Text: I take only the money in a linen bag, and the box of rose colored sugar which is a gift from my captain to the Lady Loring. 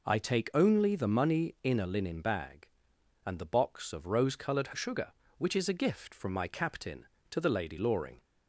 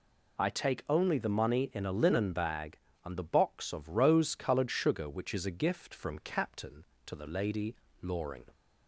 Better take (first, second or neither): first